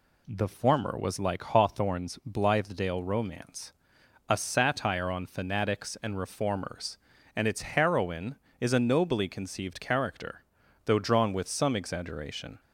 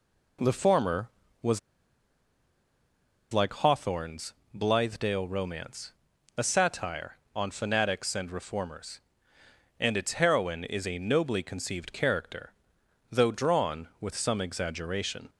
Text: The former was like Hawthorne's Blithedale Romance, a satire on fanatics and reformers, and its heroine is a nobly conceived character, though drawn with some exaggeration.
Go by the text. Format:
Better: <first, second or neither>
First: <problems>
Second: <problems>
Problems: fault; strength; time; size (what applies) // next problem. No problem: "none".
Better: first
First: none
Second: pauses between "was" and "like"; strong; at 1.5 s; 1.7 s long // pauses between "Hawthorne's" and "Blithedale"; slight; at 4.3 s; 0.20 s long